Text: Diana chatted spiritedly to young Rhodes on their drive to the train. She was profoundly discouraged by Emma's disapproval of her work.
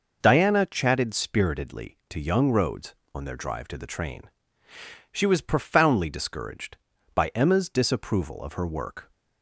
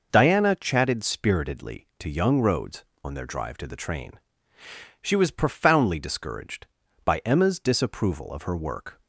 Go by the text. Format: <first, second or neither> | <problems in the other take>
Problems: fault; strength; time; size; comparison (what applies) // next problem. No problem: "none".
neither | none